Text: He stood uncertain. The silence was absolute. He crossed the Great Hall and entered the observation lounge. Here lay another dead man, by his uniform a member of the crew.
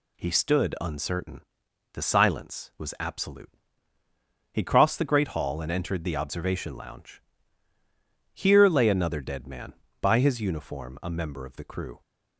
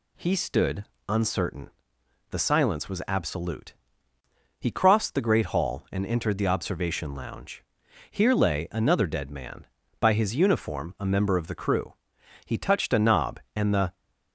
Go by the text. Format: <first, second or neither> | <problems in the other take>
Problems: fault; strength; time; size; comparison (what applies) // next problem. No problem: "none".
first | pauses between "stood" and "uncertain"; slight; at 0.8 s; 0.24 s long // goes on to say "He touched a knob and the"; from 12.4 s on; 1.5 s long